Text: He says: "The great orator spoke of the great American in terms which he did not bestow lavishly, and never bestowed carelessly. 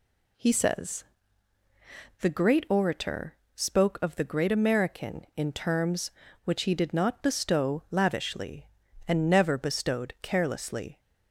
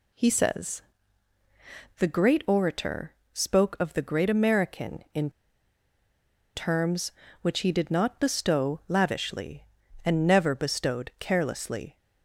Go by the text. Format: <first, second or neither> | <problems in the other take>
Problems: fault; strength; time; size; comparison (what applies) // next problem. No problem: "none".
first | pauses between "orator" and "spoke"; slight; at 3.1 s; 0.20 s long; slight in the first // pauses between "in" and "terms"; strong; at 5.2 s; 1.2 s long